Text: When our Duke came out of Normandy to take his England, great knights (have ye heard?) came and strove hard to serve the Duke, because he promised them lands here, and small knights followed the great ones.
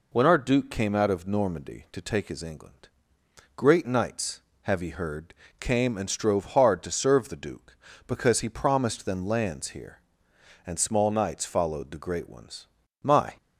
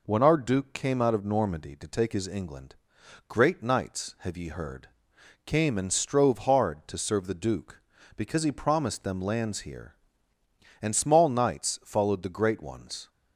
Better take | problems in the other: second | goes on to say "My"; slight; from 13.0 s on; 0.36 s long

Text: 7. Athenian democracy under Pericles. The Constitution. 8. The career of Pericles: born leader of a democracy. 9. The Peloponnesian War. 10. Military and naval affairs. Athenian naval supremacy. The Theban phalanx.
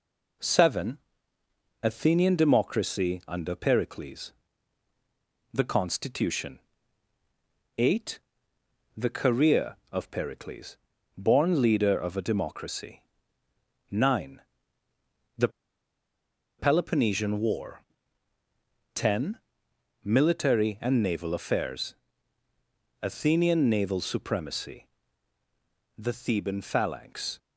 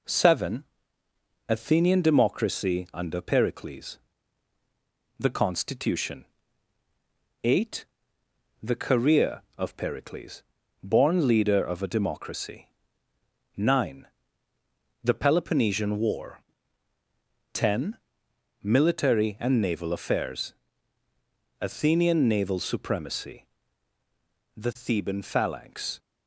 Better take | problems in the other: second | pauses between "The" and "Peloponnesian"; at 15.4 s; 1.0 s long

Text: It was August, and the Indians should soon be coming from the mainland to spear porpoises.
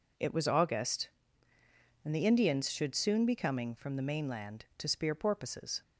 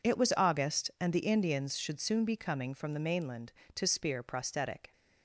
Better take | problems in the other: first | says "prosthetic" for "porpoises"; at 4.2 s

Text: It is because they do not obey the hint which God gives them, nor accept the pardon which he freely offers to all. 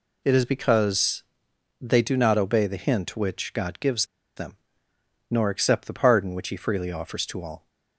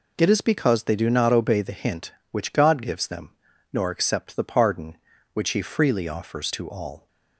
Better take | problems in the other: second | pauses between "because" and "they"; noticeable; at 1.2 s; 0.56 s long // pauses between "gives" and "them"; slight; at 4.0 s; 0.31 s long

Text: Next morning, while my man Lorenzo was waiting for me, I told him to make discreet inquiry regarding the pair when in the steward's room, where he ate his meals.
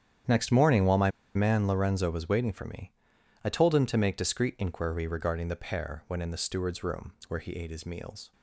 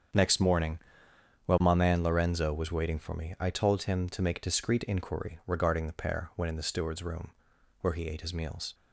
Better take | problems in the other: second | starts louder than the rest; strong; until 1.5 s; 9.5 dB; strong in the second // pauses between "my" and "man"; slight; at 1.1 s; 0.24 s long

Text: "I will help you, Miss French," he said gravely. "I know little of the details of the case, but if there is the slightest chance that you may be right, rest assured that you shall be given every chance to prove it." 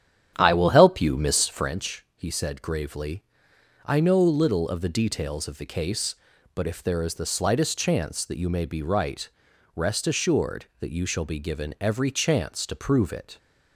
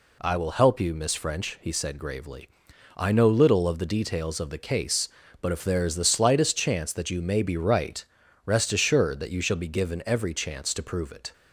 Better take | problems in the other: second | starts louder than the rest; strong; until 1.8 s; 9.5 dB

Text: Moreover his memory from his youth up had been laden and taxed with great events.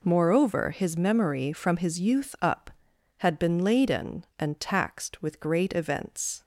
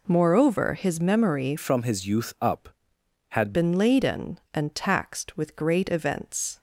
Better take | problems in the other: first | changes voice from "from" to "had"; from 1.5 to 3.5 s; 2.0 s long

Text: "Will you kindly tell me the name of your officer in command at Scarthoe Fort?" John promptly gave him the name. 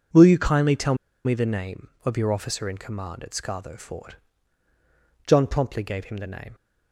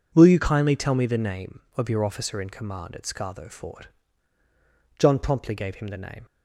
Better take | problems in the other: second | pauses between "tell" and "me"; slight; at 0.9 s; 0.30 s long

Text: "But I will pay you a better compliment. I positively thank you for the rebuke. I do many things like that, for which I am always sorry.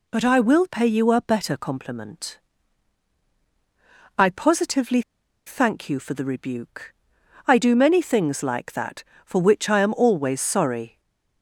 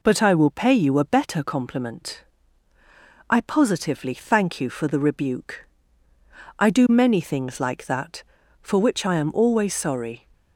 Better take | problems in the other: second | pauses between "positively" and "thank"; at 5.0 s; 0.45 s long // stays silent after the last word; slight; from 10.8 s on; 0.6 s long

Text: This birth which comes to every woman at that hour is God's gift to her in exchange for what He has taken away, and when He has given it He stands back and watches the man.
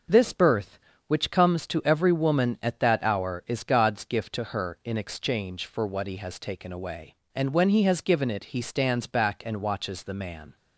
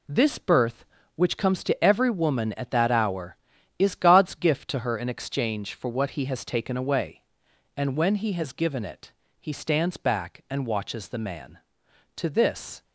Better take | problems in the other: first | pauses between "it" and "He"; slight; at 9.1 s; 0.28 s long // goes on to say "To this"; noticeable; from 12.1 s on; 0.66 s long

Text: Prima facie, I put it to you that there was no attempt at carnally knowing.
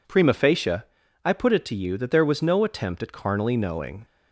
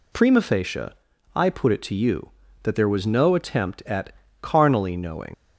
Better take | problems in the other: first | pauses between "at" and "carnally"; slight; at 4.1 s; 0.30 s long // leaves "knowing" unfinished; at 5.3 s; 90 ms

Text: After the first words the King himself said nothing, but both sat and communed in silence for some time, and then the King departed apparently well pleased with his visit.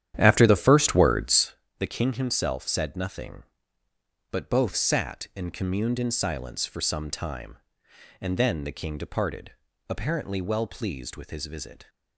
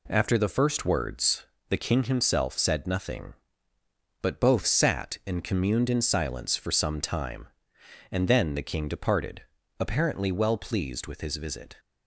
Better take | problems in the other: second | starts louder than the rest; strong; until 1.5 s; 10.5 dB // pauses between "words" and "the"; slight; at 1.5 s; 0.24 s long; slight in the second // pauses between "departed" and "apparently"; at 9.5 s; 0.38 s long; also in the second

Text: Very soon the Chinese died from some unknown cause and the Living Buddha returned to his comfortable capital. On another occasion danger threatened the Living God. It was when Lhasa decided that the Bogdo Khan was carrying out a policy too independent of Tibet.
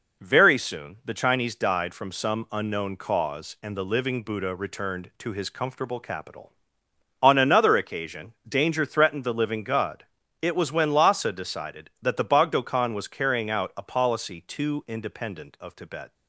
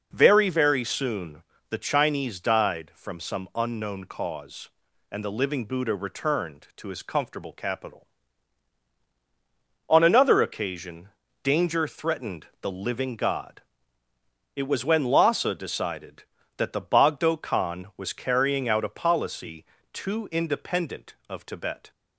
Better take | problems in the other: first | says "Very" twice; at 0.4 s // pauses between "soon" and "the"; slight; at 1.4 s; 0.28 s long // pauses between "occasion" and "danger"; slight; at 11.0 s; 0.36 s long // pauses between "policy" and "too"; slight; at 19.6 s; 0.28 s long

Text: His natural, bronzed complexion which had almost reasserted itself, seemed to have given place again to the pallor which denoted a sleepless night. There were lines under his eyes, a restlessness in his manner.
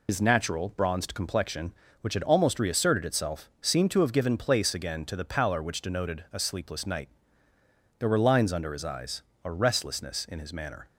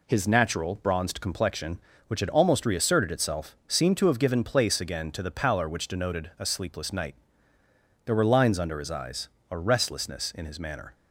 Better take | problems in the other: second | loses the start of "His"; at 0.0 s; 100 ms

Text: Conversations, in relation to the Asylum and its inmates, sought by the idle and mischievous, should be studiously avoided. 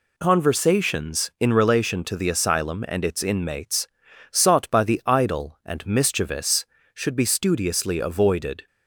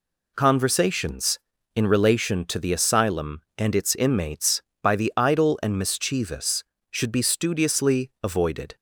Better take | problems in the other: first | skips "sought"; at 4.7 s

